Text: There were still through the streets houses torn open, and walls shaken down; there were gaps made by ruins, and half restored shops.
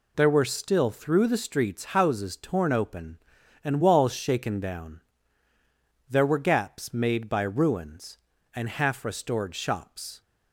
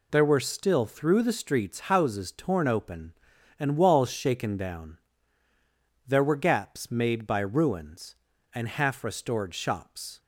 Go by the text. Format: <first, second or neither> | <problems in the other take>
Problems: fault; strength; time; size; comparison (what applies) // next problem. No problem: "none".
neither | none